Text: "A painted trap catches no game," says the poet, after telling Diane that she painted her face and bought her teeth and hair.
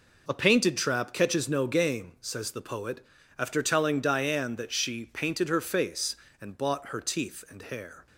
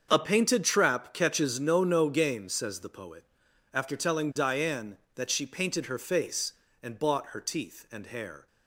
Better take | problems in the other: first | starts louder than the rest; until 1.1 s; 7 dB // says "no" twice; at 1.8 s

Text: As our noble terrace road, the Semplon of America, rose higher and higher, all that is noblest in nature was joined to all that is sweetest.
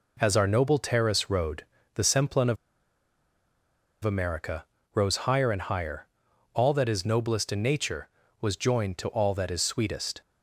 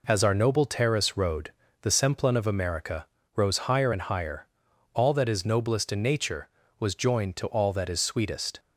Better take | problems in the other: second | pauses between "of" and "America"; strong; at 2.5 s; 1.4 s long

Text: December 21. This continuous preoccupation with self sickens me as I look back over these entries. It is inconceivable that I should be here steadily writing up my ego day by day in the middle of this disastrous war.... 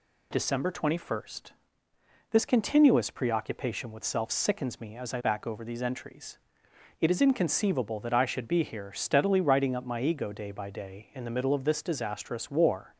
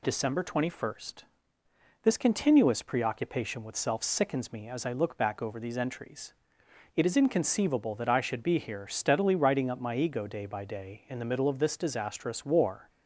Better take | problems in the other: second | skips "look"; at 5.2 s

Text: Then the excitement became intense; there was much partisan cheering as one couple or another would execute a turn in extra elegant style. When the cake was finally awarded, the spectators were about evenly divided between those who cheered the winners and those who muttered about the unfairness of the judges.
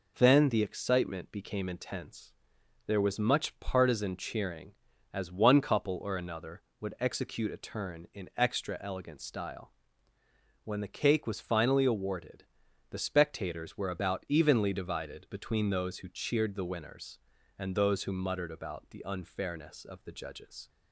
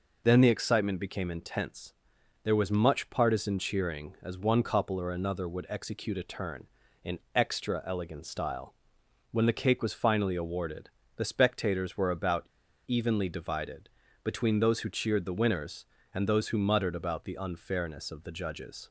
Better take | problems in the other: first | pauses between "about" and "evenly"; at 12.4 s; 0.40 s long // pauses between "divided" and "between"; slight; at 13.9 s; 0.32 s long

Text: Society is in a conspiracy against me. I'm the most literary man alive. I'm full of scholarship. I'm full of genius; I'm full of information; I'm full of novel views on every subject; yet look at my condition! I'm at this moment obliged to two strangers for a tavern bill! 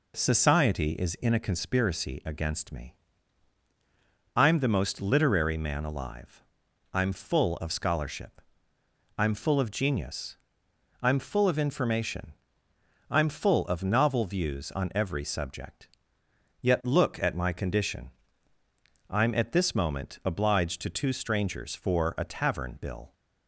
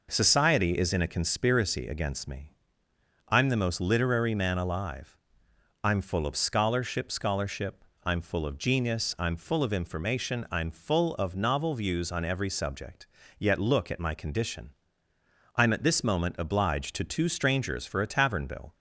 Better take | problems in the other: first | says "scholarship" twice; at 7.1 s

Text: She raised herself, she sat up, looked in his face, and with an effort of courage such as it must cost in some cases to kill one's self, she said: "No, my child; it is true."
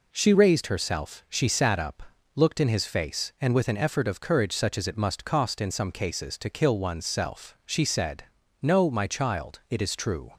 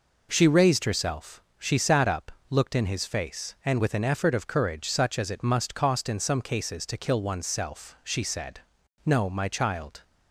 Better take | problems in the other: first | stops before "it is true"; at 10.0 s

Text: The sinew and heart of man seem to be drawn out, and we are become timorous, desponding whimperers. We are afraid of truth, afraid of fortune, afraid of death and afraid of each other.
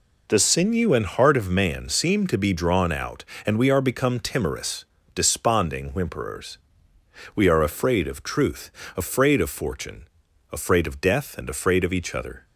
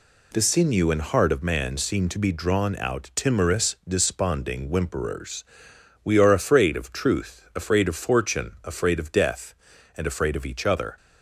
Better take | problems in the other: first | skips "and we are become"; at 3.1 s

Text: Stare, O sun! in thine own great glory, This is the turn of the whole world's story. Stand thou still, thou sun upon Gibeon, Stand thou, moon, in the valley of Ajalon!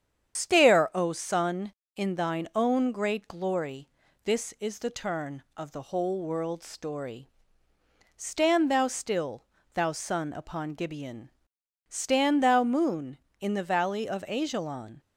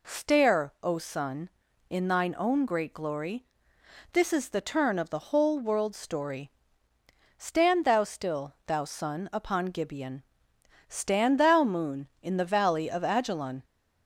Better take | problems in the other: second | loses the start of "Stare"; at 0.3 s; 110 ms // starts louder than the rest; strong; until 1.3 s; 8 dB

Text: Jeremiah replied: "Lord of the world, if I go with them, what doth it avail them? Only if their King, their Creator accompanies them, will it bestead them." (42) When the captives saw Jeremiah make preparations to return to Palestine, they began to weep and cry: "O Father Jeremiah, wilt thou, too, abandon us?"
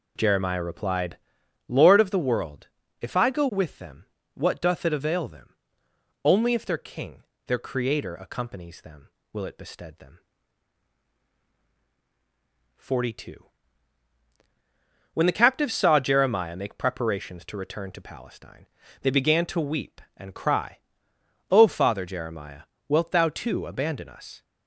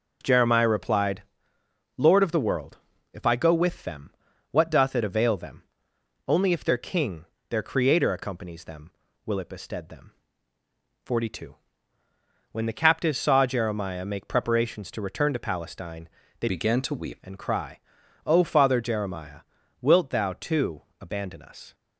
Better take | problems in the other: first | changes voice from "began" to "weep"; from 16.4 to 17.2 s; 0.8 s long

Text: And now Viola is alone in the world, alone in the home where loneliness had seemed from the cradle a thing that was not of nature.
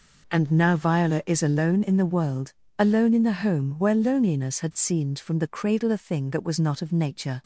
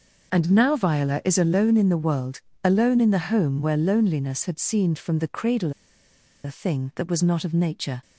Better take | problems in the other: first | pauses between "cradle" and "a"; noticeable; at 5.7 s; 0.72 s long

